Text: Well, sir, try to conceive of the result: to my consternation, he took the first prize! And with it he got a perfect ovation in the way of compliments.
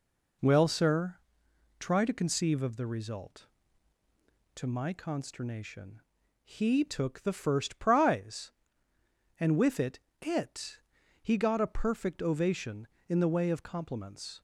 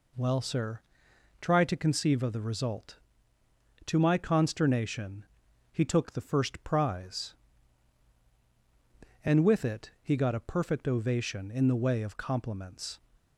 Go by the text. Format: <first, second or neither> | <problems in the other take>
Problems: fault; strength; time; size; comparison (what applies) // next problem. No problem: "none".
second | says "it" twice; at 10.2 s